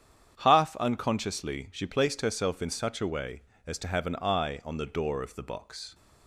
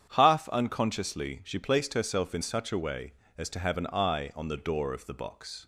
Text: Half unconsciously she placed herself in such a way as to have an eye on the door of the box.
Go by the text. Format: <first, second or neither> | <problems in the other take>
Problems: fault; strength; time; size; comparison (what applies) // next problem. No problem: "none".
neither | starts louder than the rest; strong; the same in both